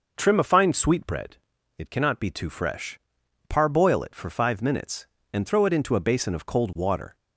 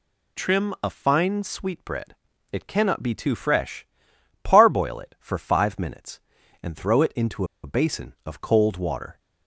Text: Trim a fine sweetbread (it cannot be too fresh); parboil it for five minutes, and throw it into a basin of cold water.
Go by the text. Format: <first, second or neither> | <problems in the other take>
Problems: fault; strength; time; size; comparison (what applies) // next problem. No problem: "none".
first | pauses between "into" and "a"; slight; at 7.4 s; 0.19 s long